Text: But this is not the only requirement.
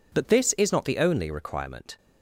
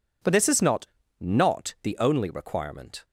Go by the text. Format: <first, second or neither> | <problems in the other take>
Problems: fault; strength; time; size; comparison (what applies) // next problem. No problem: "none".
first | says "not" twice; at 1.2 s